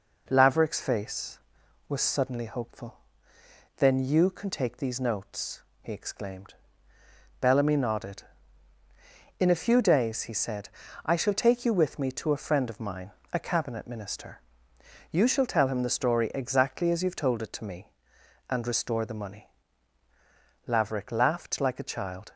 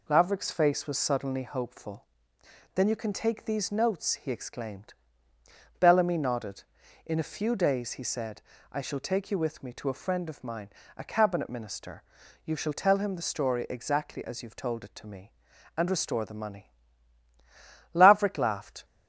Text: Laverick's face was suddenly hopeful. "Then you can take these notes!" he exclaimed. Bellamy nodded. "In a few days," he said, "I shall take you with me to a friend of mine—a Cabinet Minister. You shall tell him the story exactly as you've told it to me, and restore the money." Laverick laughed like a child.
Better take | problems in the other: first | stops before "like a child"; at 18.8 s

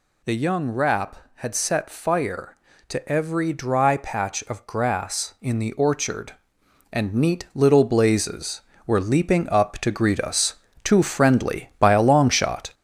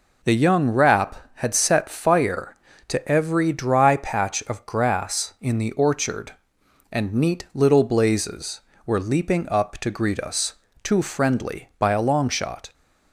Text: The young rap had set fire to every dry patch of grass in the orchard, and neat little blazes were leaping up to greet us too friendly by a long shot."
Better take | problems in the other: second | gets louder; noticeable; throughout; 5.5 dB // pauses between "us" and "too"; slight; at 10.5 s; 0.30 s long; slight in the second

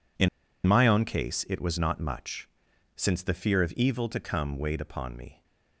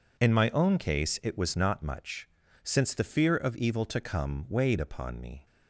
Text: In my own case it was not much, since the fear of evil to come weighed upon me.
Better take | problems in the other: second | pauses between "In" and "my"; at 0.2 s; 0.38 s long

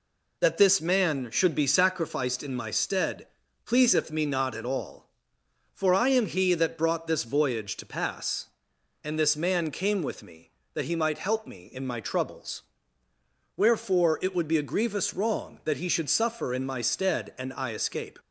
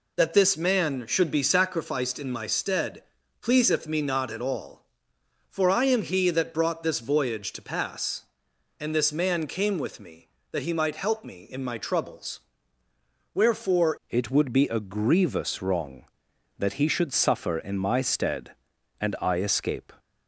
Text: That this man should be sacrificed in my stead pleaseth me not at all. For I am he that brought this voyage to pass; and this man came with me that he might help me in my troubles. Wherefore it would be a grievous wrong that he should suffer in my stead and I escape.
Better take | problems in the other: first | pauses between "stead" and "pleaseth"; at 3.0 s; 0.38 s long; also in the first // changes voice at "it"; from 14.0 s on; 5.9 s long

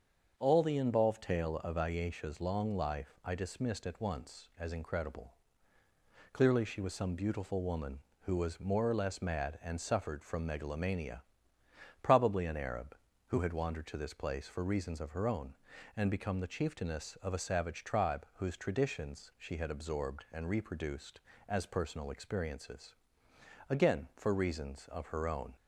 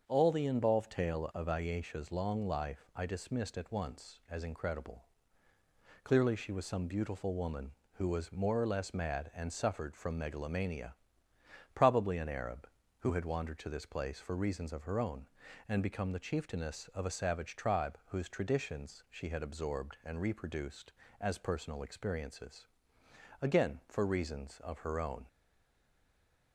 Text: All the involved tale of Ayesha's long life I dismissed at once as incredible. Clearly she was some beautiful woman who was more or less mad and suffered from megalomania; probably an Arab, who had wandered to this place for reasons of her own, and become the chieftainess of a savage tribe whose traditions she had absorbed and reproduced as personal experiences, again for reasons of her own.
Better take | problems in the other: first | starts louder than the rest; until 1.0 s; 6.5 dB; also in the first // stays silent after the last word; noticeable; from 25.2 s on; 1.3 s long

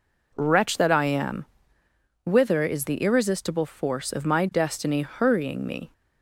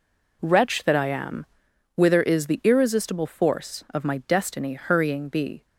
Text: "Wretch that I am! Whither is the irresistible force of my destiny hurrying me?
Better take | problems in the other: first | says "be" for "me"; at 5.2 s

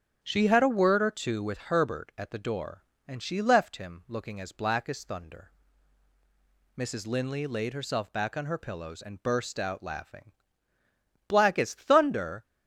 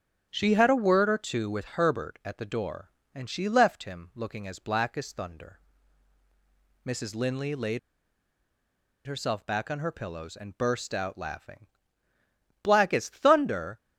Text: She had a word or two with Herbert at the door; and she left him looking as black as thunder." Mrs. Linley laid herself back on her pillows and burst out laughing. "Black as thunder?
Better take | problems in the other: first | starts louder than the rest; strong; until 1.3 s; 7 dB; strong in the first // pauses between "laid" and "herself"; strong; at 7.7 s; 1.2 s long

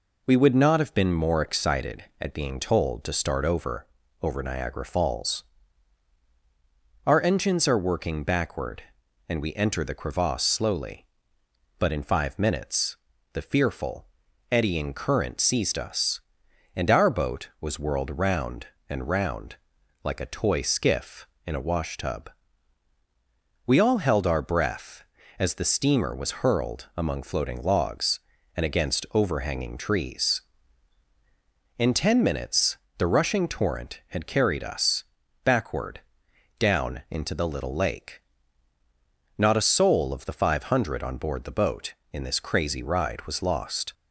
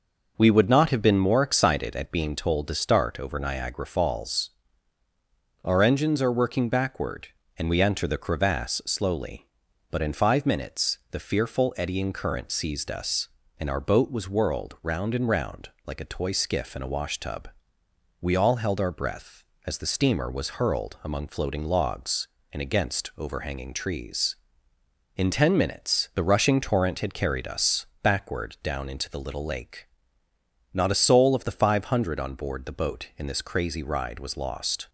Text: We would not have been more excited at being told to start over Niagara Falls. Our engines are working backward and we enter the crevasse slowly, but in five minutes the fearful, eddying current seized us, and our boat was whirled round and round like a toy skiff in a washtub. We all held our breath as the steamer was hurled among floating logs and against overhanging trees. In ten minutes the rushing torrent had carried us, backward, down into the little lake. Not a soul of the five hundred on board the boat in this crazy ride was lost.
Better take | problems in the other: second | says "over" twice; at 4.2 s // pauses between "minutes" and "the"; slight; at 12.9 s; 0.36 s long // pauses between "round" and "like"; noticeable; at 19.5 s; 0.48 s long; slight in the second // pauses between "minutes" and "the"; slight; at 32.7 s; 0.20 s long

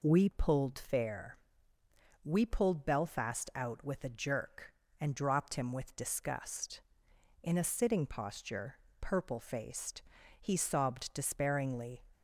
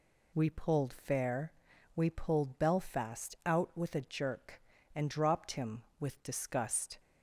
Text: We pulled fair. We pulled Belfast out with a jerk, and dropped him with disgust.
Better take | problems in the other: second | goes on to say "In a sitting posture purple faced he sobbed despairingly"; strong; from 7.4 s on; 4.6 s long

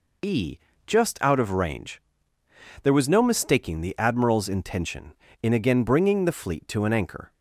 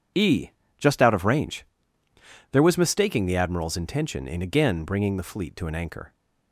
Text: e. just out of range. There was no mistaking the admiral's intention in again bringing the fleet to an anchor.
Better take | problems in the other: first | skips "no"; at 2.7 s

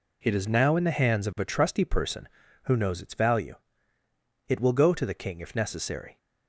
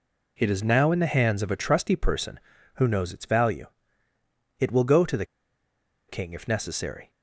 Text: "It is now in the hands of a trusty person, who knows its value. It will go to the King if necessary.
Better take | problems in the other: first | pauses between "the" and "King"; noticeable; at 5.2 s; 0.83 s long

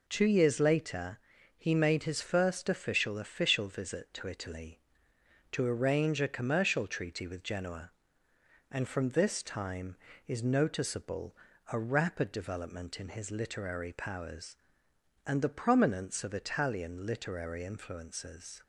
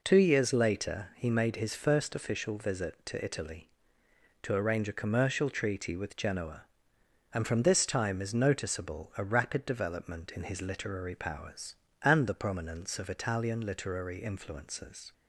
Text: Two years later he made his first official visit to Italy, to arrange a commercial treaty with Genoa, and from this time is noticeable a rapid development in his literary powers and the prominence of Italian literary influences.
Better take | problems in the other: second | pauses between "later" and "he"; at 1.1 s; 0.38 s long // says "official" twice; at 3.1 s // pauses between "noticeable" and "a"; slight; at 11.3 s; 0.34 s long

